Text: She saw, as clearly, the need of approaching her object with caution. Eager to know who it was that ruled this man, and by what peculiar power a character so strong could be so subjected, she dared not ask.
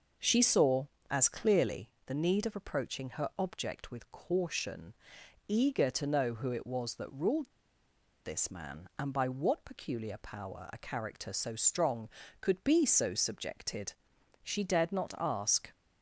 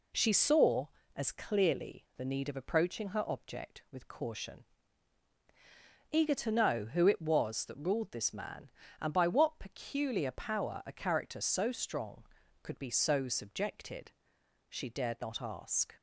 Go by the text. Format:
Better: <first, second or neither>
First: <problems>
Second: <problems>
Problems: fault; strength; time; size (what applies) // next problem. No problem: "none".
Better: second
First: pauses between "ruled" and "this"; noticeable; at 7.5 s; 0.74 s long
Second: none